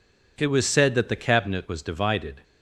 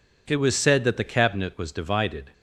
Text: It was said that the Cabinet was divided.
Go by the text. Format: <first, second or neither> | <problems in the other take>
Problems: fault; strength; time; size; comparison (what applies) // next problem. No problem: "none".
neither | none